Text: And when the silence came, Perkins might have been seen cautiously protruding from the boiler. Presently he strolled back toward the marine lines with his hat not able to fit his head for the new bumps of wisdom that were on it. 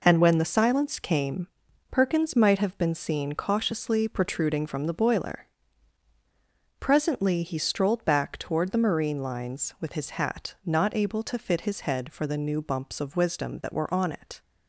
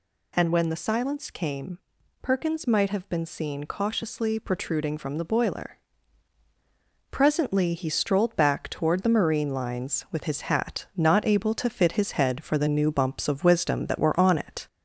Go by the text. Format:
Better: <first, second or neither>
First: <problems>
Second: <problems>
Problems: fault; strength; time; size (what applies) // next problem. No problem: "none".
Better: first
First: none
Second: gets louder; slight; throughout; 3 dB